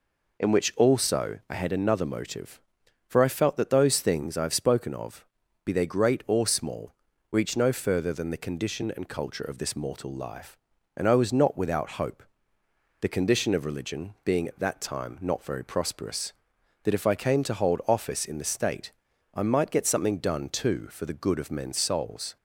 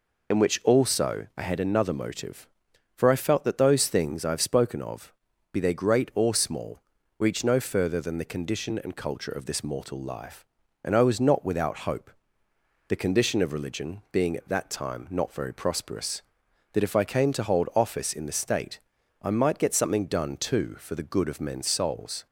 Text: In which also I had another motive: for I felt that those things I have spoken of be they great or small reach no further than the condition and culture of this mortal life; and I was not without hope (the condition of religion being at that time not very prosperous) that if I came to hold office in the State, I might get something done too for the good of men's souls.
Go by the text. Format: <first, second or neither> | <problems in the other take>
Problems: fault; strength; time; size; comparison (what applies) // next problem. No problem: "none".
first | loses the start of "In"; at 0.3 s; 30 ms // pauses between "of" and "be"; at 5.1 s; 0.40 s long; also in the first // pauses between "small" and "reach"; at 6.7 s; 0.38 s long; also in the first